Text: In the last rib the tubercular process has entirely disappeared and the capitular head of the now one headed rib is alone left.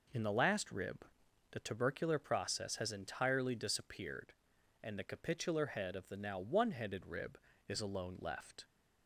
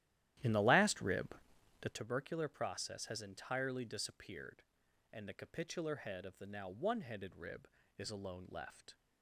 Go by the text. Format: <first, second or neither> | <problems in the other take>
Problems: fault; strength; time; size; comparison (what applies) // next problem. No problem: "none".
first | starts louder than the rest; strong; until 2.0 s; 13 dB // pauses between "rib" and "the"; noticeable; at 1.3 s; 0.46 s long; noticeable in the first